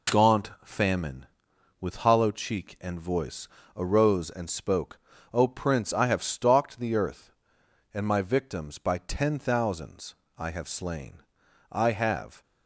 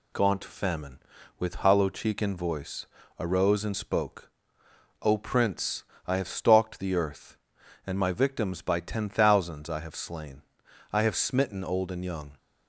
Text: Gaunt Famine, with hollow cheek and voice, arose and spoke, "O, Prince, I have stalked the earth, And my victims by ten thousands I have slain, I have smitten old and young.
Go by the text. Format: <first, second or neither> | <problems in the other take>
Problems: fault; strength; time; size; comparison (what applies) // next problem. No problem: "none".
second | pauses between "thousands" and "I"; slight; at 10.1 s; 0.24 s long // stops before "smitten old and young"; at 12.4 s